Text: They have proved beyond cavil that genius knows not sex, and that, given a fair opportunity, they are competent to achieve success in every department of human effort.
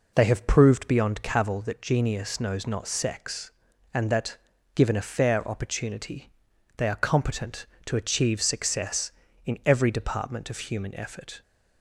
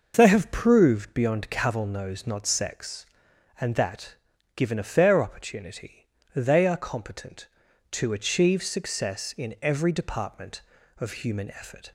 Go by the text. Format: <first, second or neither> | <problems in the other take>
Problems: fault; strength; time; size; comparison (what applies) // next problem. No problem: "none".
first | skips "that genius"; at 1.8 s